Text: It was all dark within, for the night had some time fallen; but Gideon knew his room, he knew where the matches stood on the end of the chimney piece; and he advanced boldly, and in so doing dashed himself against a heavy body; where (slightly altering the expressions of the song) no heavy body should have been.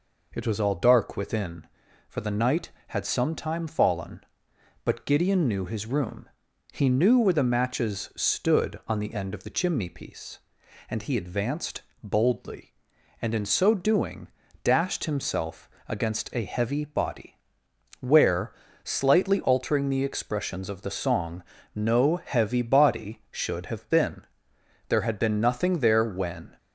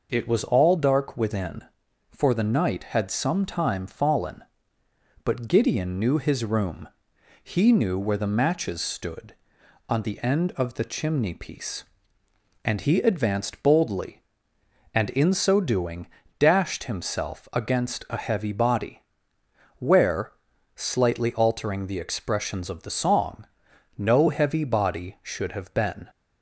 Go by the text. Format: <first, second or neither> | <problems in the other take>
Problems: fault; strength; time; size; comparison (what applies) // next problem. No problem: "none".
second | pauses between "advanced" and "boldly"; slight; at 11.8 s; 0.20 s long // pauses between "doing" and "dashed"; slight; at 14.2 s; 0.36 s long; slight in the second // pauses between "himself" and "against"; slight; at 15.6 s; 0.18 s long // goes on to say "There had been nothing there when"; strong; from 24.8 s on; 1.6 s long